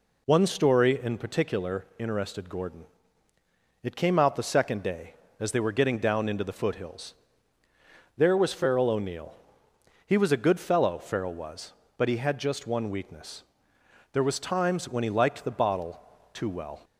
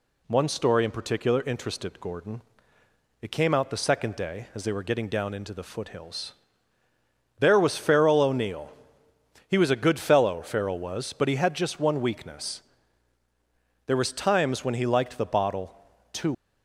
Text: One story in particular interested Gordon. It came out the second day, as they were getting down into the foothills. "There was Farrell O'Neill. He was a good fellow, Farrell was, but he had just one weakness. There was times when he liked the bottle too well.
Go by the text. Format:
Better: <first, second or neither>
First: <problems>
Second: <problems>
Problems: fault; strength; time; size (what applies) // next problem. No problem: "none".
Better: first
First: pauses between "bottle" and "too"; slight; at 15.9 s; 0.32 s long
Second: pauses between "bottle" and "too"; slight; at 15.7 s; 0.36 s long // stops before "well"; at 16.3 s